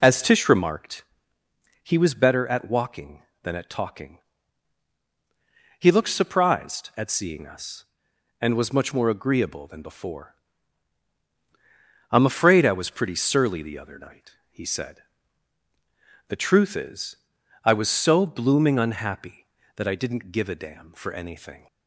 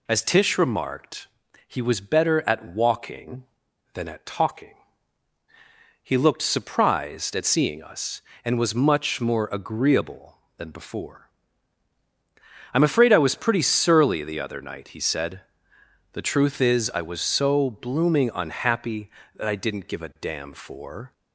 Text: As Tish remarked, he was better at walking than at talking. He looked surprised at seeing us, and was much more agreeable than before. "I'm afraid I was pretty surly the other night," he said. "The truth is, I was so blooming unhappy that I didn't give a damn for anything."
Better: first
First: none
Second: stops before "anything"; at 21.1 s

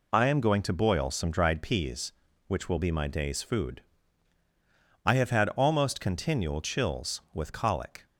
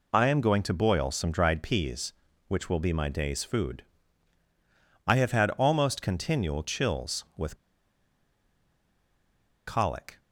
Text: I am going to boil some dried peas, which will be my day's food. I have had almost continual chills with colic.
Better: first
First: none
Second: pauses between "with" and "colic"; strong; at 7.5 s; 2.1 s long

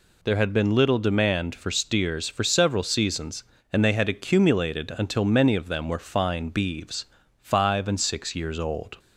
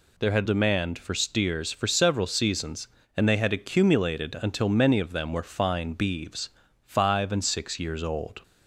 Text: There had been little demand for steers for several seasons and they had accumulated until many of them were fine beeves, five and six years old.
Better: first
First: none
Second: skips "been little"; at 0.4 s

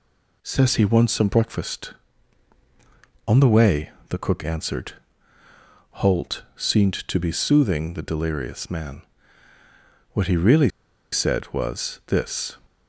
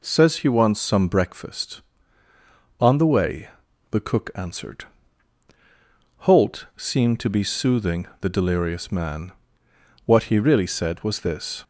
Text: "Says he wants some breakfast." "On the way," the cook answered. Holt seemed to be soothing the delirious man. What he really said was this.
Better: second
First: pauses between "really" and "said"; at 10.6 s; 0.42 s long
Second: none

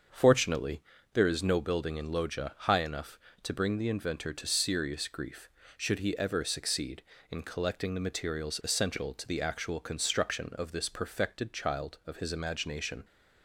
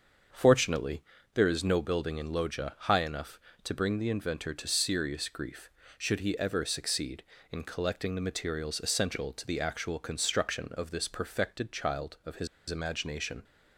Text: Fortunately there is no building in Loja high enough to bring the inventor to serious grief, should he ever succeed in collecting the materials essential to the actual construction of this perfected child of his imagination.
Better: first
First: starts louder than the rest; until 1.4 s; 6.5 dB // pauses between "Fortunately" and "there"; slight; at 0.8 s; 0.30 s long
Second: starts louder than the rest; until 1.6 s; 6.5 dB // pauses between "Fortunately" and "there"; slight; at 1.0 s; 0.30 s long // pauses between "his" and "imagination"; slight; at 12.4 s; 0.22 s long

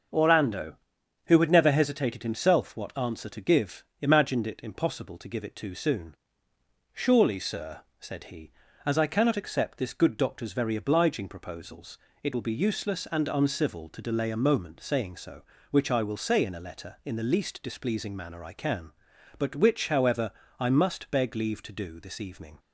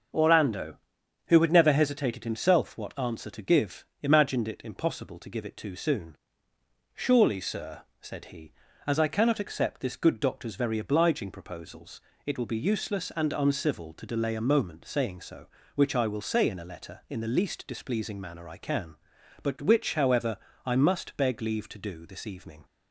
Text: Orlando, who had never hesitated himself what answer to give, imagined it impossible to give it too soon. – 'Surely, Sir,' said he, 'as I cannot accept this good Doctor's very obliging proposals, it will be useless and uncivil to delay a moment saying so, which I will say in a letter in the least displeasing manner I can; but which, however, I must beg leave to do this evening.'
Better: neither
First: starts louder than the rest; until 1.6 s; 6.5 dB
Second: starts louder than the rest; until 1.6 s; 6.5 dB

